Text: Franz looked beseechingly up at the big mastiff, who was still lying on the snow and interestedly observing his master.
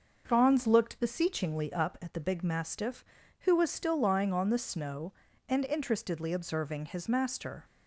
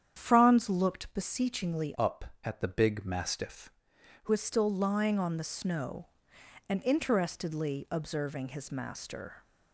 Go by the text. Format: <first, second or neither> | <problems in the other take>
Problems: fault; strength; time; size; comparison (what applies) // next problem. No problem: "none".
first | starts louder than the rest; strong; until 1.1 s; 9 dB; noticeable in the first // changes voice from "up" to "who"; from 1.9 to 4.3 s; 2.4 s long